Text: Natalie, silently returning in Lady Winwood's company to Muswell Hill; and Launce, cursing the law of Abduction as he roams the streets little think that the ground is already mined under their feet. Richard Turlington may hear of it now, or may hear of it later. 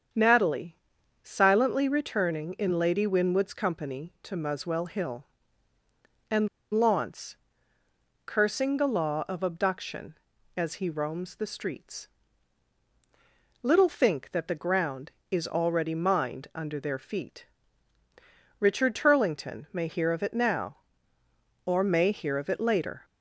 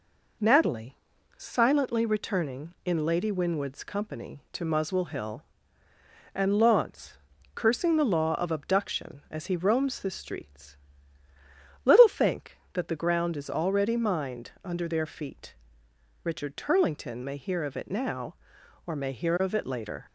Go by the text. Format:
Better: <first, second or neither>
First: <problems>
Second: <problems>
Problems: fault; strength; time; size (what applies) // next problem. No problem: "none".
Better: second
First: starts louder than the rest; strong; until 1.6 s; 7 dB // pauses between "and" and "Launce"; slight; at 6.4 s; 0.24 s long // pauses between "streets" and "little"; strong; at 12.0 s; 1.5 s long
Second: pauses between "streets" and "little"; at 10.7 s; 1.0 s long